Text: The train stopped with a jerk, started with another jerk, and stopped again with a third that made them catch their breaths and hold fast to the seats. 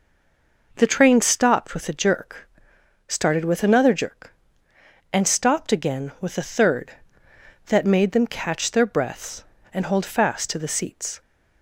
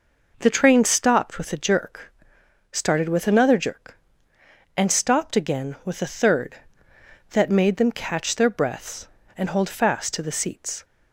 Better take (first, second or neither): second